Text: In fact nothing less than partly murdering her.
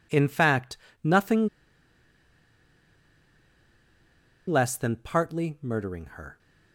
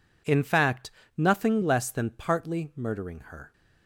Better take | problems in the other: second | pauses between "fact" and "nothing"; slight; at 0.7 s; 0.24 s long; slight in the second // pauses between "nothing" and "less"; strong; at 1.4 s; 2.9 s long

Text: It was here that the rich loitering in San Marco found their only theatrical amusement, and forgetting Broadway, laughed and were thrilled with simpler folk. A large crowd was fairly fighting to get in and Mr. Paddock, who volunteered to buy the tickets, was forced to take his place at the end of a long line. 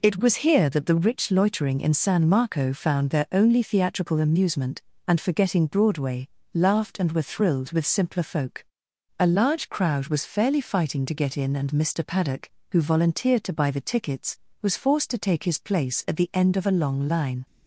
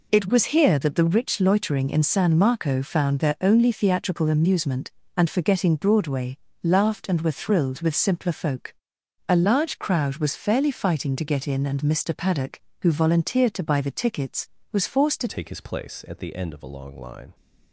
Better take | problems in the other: first | changes voice at "take"; from 15.2 s on; 2.1 s long

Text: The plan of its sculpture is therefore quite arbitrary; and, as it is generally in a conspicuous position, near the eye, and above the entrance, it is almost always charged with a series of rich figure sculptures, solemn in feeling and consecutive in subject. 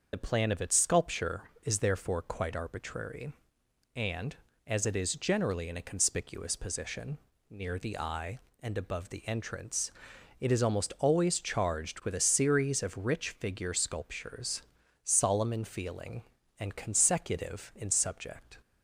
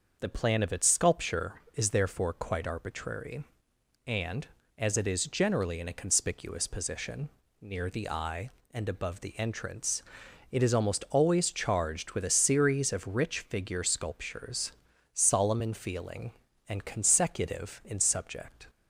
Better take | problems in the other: second | loses the start of "The"; at 0.1 s; 40 ms // starts louder than the rest; until 1.1 s; 6 dB; also in the second

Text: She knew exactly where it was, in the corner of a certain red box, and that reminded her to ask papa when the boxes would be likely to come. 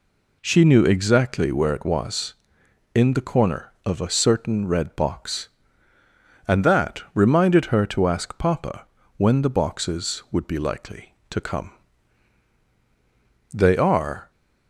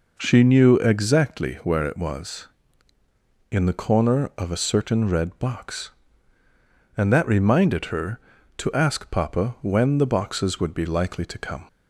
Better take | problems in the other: second | pauses between "papa" and "when"; slight; at 8.8 s; 0.30 s long // goes on to say "They are"; noticeable; from 13.5 s on; 0.78 s long

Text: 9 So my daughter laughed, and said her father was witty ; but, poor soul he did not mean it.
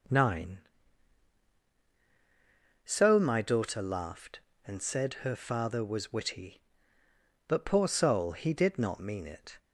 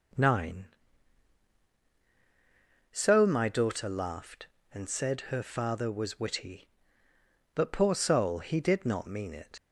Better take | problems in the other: first | leaves "it" unfinished; at 9.5 s; 70 ms

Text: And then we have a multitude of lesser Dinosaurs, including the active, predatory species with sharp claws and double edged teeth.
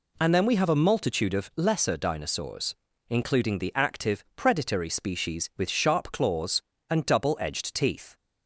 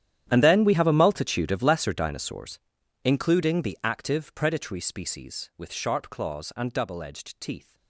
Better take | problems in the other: first | gets quieter; strong; throughout; 19 dB

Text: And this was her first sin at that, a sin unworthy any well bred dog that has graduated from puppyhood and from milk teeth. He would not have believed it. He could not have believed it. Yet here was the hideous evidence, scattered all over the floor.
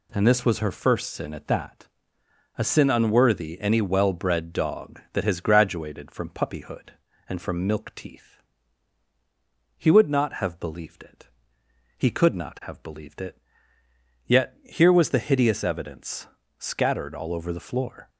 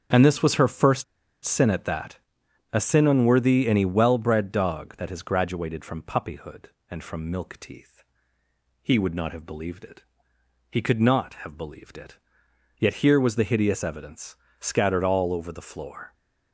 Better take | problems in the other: first | starts louder than the rest; strong; until 1.5 s; 8 dB // pauses between "first" and "sin"; at 1.0 s; 0.40 s long

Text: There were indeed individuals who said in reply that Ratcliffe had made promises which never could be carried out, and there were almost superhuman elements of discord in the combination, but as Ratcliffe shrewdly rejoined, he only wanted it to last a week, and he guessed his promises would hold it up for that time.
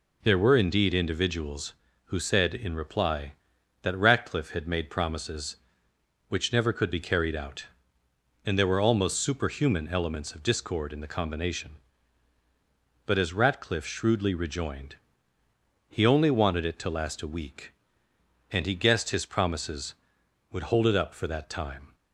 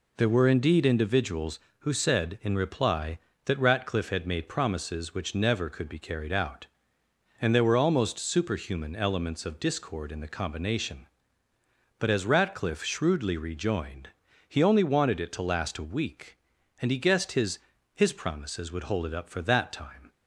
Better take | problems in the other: first | says "his" twice; at 17.9 s

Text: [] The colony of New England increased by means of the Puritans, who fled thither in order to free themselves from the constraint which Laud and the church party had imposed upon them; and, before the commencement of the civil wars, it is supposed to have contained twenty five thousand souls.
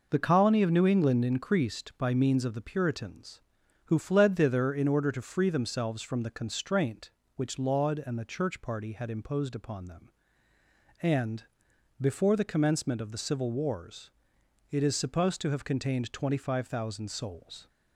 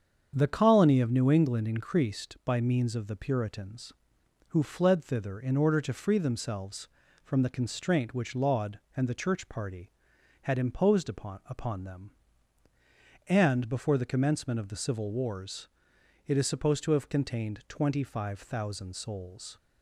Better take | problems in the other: first | starts louder than the rest; strong; until 1.3 s; 7.5 dB // says "upon" twice; at 11.4 s

